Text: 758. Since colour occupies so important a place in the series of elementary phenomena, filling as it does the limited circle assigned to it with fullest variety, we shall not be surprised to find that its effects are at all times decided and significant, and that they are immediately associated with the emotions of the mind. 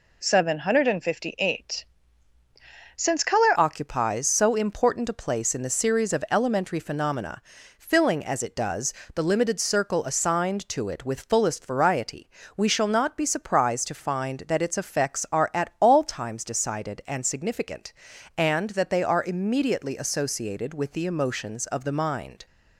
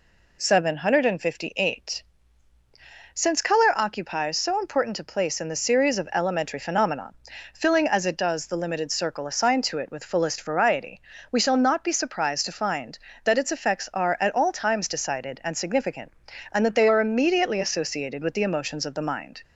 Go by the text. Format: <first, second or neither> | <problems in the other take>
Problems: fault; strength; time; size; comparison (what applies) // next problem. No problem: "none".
second | changes voice at "occupies"; from 3.5 s on; 18.9 s long // pauses between "does" and "the"; slight; at 8.9 s; 0.22 s long